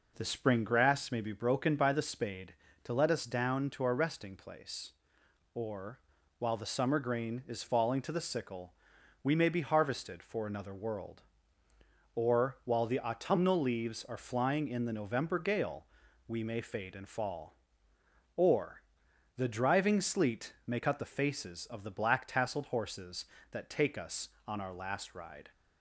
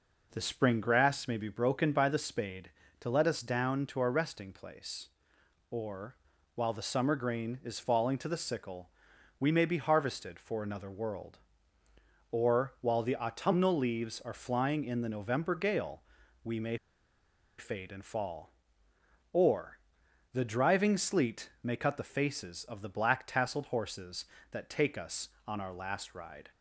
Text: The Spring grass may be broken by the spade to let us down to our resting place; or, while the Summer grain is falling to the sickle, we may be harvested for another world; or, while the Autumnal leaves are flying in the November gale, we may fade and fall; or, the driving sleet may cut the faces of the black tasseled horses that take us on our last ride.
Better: first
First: none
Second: pauses between "may" and "fade"; noticeable; at 16.7 s; 0.81 s long

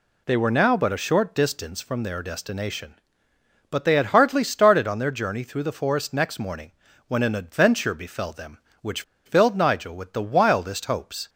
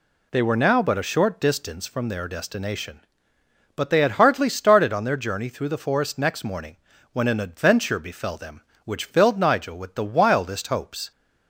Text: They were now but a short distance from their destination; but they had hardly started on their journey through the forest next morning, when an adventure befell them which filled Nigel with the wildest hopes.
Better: second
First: pauses between "which" and "filled"; slight; at 9.0 s; 0.23 s long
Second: none

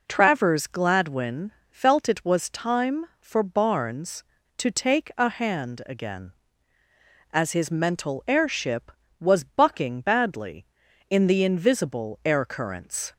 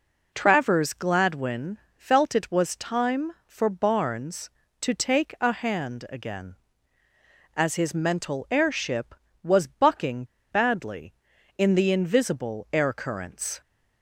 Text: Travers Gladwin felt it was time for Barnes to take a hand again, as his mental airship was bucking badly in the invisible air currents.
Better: first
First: pauses between "Gladwin" and "felt"; slight; at 1.5 s; 0.18 s long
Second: pauses between "Gladwin" and "felt"; slight; at 1.7 s; 0.18 s long // pauses between "bucking" and "badly"; slight; at 10.2 s; 0.27 s long

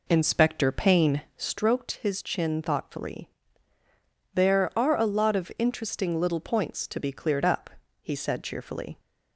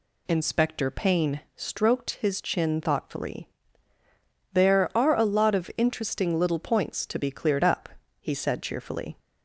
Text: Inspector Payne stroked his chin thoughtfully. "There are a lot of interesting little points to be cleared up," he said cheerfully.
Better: second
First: starts louder than the rest; until 1.6 s; 3.5 dB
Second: none

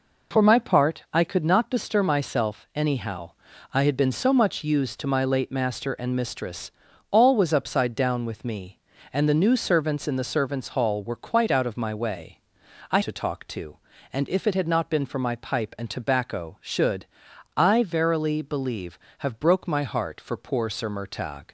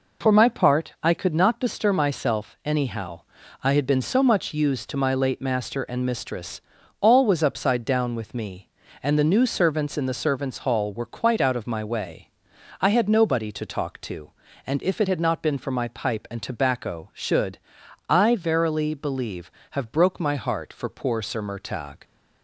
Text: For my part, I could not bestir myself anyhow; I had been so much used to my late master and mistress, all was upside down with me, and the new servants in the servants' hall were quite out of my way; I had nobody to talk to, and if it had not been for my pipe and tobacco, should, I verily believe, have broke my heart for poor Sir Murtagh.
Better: second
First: skips "had nobody"; at 13.0 s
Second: none

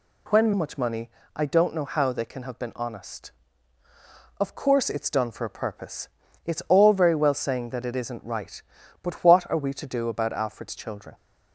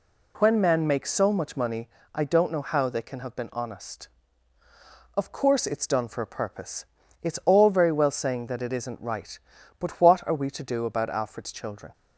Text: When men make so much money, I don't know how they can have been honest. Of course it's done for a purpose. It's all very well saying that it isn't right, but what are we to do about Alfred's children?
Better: second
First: skips "men make so"; at 0.5 s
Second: none

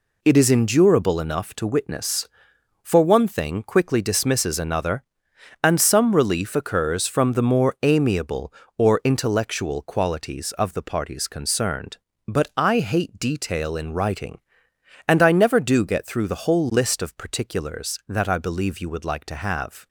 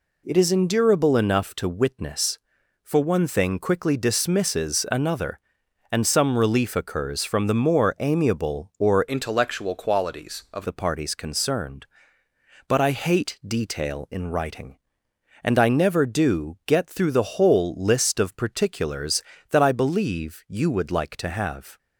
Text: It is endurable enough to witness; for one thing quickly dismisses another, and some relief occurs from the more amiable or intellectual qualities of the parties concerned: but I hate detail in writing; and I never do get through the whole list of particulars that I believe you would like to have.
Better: first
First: none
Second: changes voice from "intellectual" to "of"; from 9.0 to 10.6 s; 1.6 s long

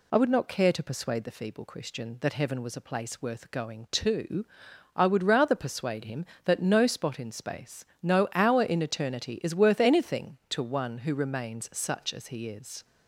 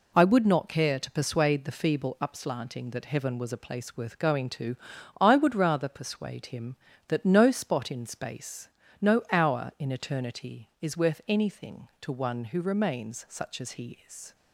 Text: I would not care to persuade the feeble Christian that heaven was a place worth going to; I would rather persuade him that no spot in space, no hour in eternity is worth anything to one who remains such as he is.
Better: first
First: none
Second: says "Upslanting" for "Christian"; at 2.2 s

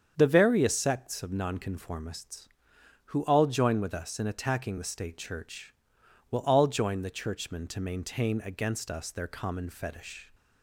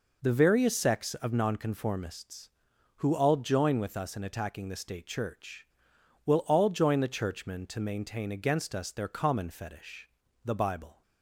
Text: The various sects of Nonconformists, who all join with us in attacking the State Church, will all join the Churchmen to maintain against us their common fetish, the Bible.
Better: second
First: starts louder than the rest; strong; until 1.1 s; 7.5 dB // stops before "the Bible"; at 10.3 s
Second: none

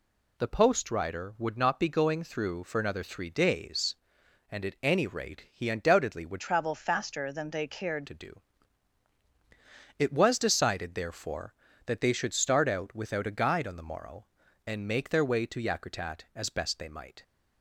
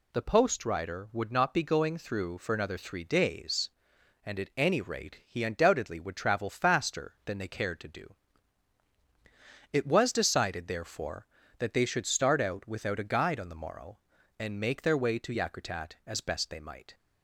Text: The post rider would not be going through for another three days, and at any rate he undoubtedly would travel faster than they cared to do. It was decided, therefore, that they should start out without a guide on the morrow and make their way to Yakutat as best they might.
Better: second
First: changes voice from "travel" to "cared"; from 6.4 to 8.0 s; 1.6 s long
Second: none

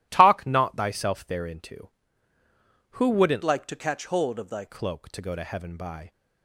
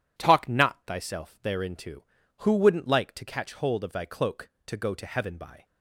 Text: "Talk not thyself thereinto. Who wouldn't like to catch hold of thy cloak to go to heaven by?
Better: second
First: changes voice from "like" to "thy"; from 3.4 to 4.6 s; 1.2 s long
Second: none

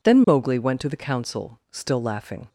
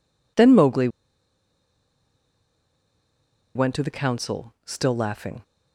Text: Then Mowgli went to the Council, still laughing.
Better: first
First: none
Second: pauses between "Mowgli" and "went"; strong; at 0.8 s; 2.6 s long

